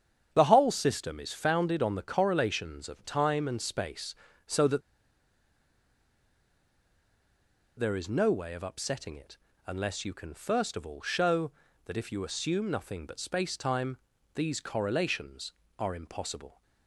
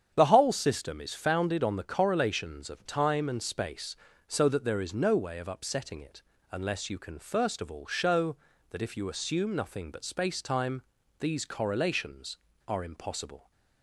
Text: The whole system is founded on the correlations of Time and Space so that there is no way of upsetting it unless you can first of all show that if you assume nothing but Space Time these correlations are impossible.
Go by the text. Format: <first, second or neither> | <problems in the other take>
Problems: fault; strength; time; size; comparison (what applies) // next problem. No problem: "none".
second | starts louder than the rest; strong; until 1.3 s; 8.5 dB; strong in the second // pauses between "that" and "there"; strong; at 4.8 s; 2.9 s long // pauses between "it" and "unless"; slight; at 9.3 s; 0.30 s long; slight in the second // pauses between "Time" and "these"; at 13.9 s; 0.38 s long; also in the second